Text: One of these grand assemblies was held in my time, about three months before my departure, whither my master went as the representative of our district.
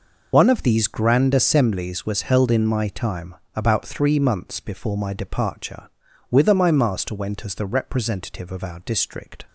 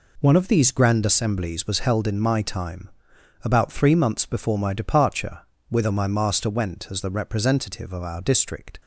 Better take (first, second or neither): second